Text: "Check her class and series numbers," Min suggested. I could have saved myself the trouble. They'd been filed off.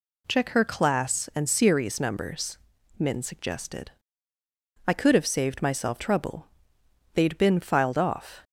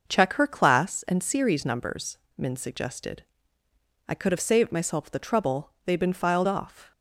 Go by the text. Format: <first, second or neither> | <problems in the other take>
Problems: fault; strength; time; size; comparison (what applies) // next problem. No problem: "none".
second | skips "the"; at 5.9 s